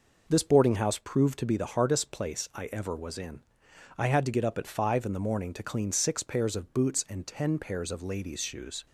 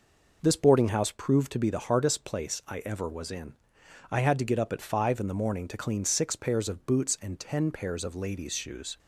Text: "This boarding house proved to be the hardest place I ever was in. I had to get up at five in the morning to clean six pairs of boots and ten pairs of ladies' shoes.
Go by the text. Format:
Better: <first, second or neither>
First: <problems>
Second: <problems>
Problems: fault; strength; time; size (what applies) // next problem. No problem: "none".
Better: neither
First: none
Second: none